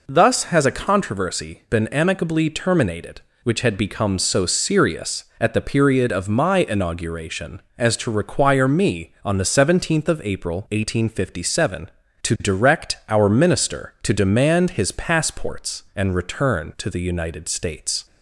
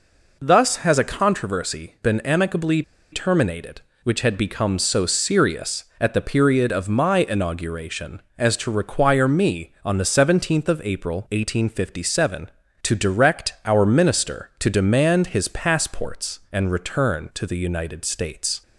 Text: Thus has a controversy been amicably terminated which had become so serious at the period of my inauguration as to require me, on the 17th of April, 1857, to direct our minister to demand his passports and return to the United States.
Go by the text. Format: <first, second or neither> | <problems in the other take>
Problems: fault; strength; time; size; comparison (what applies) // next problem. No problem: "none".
first | pauses between "amicably" and "terminated"; slight; at 2.8 s; 0.31 s long